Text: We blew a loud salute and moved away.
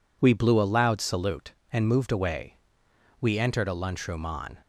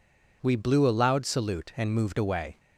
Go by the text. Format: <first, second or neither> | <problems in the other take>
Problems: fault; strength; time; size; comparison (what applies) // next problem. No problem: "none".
second | goes on to say "We entered a lunchroom on"; from 3.2 s on; 1.3 s long